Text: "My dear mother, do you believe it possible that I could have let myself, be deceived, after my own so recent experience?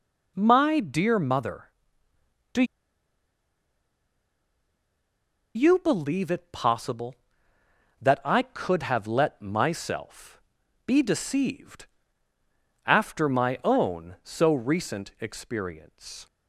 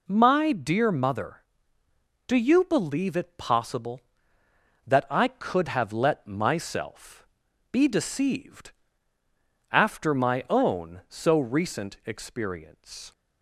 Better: second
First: pauses between "do" and "you"; strong; at 2.6 s; 2.9 s long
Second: none

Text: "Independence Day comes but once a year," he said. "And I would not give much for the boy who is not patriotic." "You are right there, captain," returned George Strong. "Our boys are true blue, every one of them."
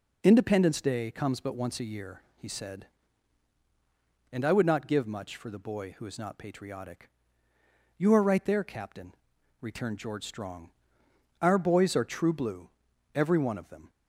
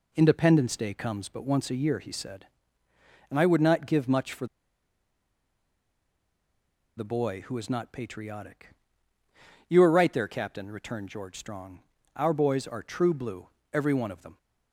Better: first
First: none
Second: pauses between "for" and "the"; strong; at 4.4 s; 2.5 s long

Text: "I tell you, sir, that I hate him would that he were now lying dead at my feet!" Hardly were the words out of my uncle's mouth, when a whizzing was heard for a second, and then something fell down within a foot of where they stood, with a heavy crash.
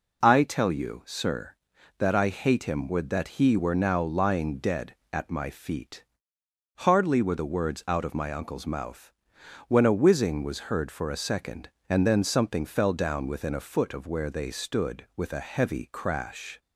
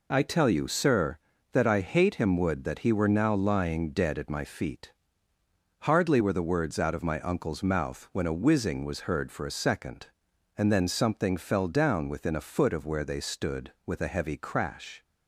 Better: neither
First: none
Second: none

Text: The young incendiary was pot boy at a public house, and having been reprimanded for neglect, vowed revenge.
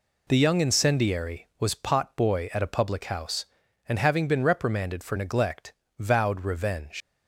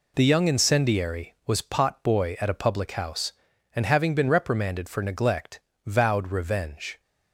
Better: second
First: leaves "revenge" unfinished; at 7.0 s; 120 ms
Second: none

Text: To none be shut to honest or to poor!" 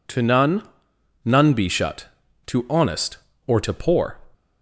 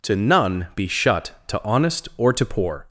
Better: second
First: says "none" twice; at 1.2 s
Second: none

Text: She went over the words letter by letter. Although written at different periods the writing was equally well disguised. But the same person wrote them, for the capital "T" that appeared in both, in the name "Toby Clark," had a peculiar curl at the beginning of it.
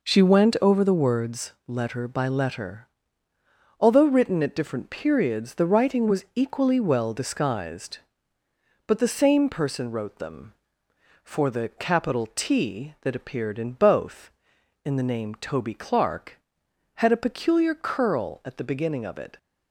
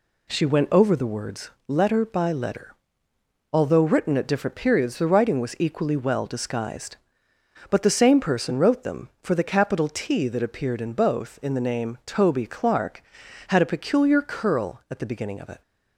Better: neither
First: pauses between "words" and "letter"; slight; at 1.5 s; 0.16 s long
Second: pauses between "words" and "letter"; slight; at 1.4 s; 0.18 s long

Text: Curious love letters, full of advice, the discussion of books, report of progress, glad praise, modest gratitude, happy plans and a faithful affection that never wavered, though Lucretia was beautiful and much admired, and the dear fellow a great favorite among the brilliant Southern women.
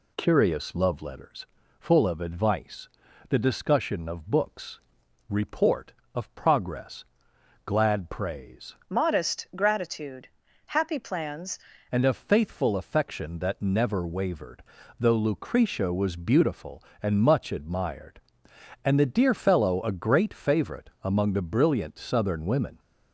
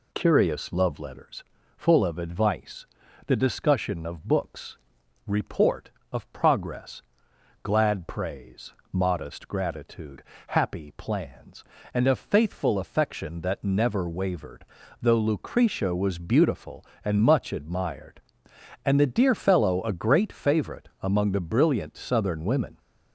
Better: second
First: changes voice from "modest" to "plans"; from 8.8 to 11.5 s; 2.7 s long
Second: none

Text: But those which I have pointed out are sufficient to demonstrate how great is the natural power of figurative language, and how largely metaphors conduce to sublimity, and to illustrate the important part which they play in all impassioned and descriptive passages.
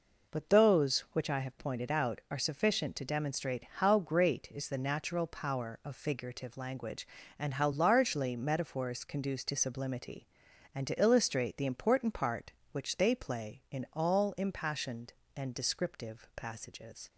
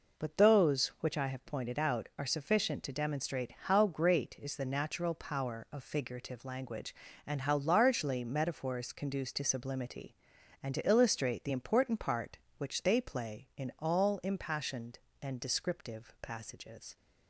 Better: neither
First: none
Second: none

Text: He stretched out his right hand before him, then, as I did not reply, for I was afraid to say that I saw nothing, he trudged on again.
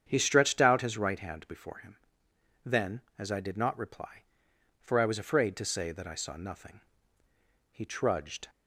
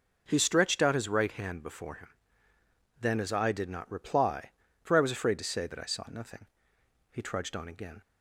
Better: second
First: starts louder than the rest; strong; until 1.0 s; 8 dB // stops before "on again"; at 8.4 s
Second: none

